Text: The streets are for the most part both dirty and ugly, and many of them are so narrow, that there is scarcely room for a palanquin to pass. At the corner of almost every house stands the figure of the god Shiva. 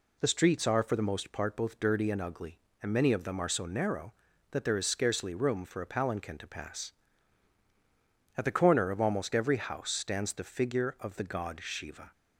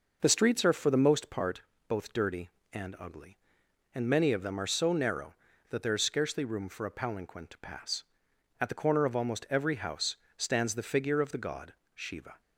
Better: first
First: none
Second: starts louder than the rest; noticeable; until 1.6 s; 6 dB // pauses between "part" and "both"; slight; at 1.6 s; 0.26 s long // pauses between "house" and "stands"; slight; at 10.1 s; 0.20 s long // pauses between "god" and "Shiva"; slight; at 11.7 s; 0.20 s long

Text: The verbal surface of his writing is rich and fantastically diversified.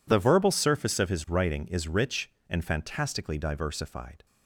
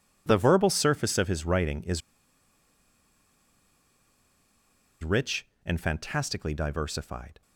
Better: first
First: none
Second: pauses between "is" and "rich"; strong; at 2.0 s; 3.0 s long

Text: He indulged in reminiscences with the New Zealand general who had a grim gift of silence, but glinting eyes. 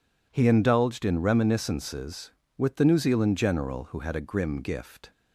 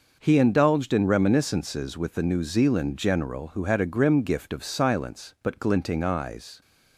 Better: second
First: stops before "of silence but glinting eyes"; at 5.1 s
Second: none

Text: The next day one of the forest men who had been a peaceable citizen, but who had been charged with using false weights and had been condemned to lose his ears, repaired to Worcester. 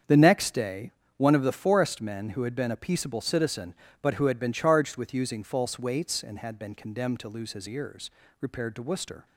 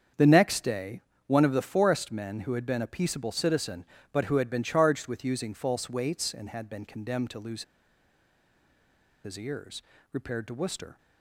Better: first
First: starts louder than the rest; strong; until 1.3 s; 7.5 dB // pauses between "day" and "one"; slight; at 0.9 s; 0.24 s long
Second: starts louder than the rest; strong; until 1.4 s; 7.5 dB // pauses between "day" and "one"; slight; at 1.0 s; 0.24 s long // pauses between "lose" and "his"; strong; at 7.6 s; 1.6 s long

